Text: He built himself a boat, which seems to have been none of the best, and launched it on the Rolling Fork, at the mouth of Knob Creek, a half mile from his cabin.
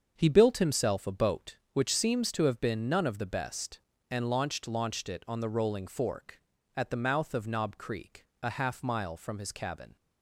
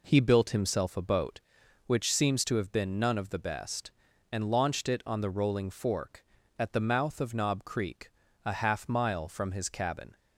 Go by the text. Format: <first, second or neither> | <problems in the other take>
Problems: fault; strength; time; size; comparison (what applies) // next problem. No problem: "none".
second | starts louder than the rest; until 1.1 s; 7 dB // says "launched" twice; at 4.6 s